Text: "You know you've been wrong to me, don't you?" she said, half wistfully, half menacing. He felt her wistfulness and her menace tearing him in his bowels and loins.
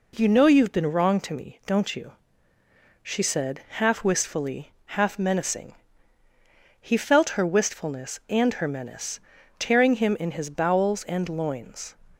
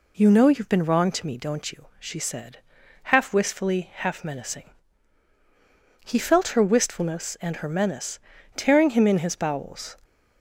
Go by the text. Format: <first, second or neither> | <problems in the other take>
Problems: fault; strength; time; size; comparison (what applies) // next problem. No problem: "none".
first | pauses between "menace" and "tearing"; slight; at 8.2 s; 0.34 s long; also in the first // stops before "and loins"; at 10.0 s